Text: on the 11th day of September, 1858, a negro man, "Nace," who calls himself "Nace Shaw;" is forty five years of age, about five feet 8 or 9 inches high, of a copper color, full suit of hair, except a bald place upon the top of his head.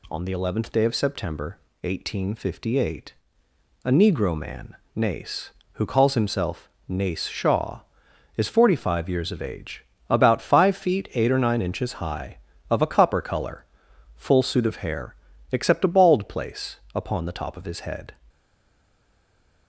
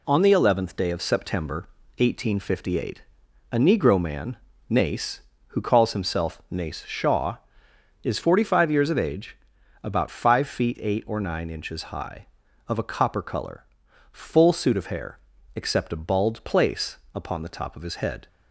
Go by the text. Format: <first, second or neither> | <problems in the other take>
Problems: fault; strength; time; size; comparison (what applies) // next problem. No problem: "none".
second | pauses between "himself" and "Nace"; slight; at 6.6 s; 0.18 s long // pauses between "place" and "upon"; slight; at 16.7 s; 0.18 s long; slight in the second // stays silent after the last word; noticeable; from 18.2 s on; 1.4 s long